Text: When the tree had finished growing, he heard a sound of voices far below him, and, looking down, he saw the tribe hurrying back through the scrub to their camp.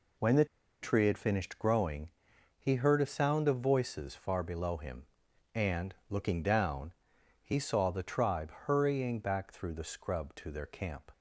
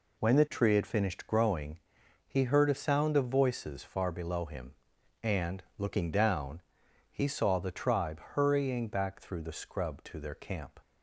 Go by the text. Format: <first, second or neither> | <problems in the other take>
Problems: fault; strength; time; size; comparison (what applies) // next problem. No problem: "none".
second | pauses between "the" and "tree"; at 0.4 s; 0.37 s long